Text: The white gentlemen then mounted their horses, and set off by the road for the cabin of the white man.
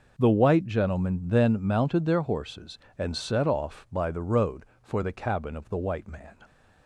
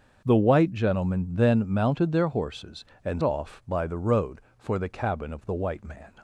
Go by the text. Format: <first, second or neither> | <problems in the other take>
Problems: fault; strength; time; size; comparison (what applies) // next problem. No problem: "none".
first | starts louder than the rest; until 1.2 s; 6.5 dB // skips "set"; at 3.2 s